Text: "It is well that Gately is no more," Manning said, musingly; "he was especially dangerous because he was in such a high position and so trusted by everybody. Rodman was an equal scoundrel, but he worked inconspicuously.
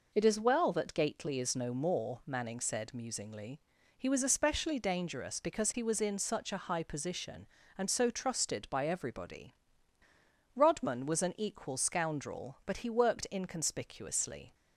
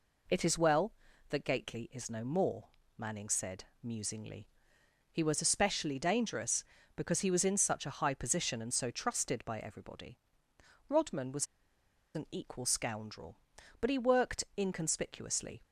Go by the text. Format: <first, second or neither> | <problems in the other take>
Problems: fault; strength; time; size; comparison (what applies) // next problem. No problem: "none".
first | pauses between "was" and "an"; noticeable; at 11.4 s; 0.69 s long